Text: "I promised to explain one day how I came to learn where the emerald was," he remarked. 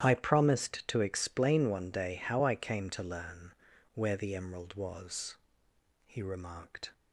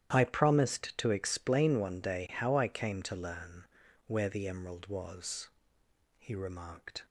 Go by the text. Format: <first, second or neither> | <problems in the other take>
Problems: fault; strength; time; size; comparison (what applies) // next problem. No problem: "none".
neither | starts louder than the rest; strong; the same in both // pauses between "learn" and "where"; the same in both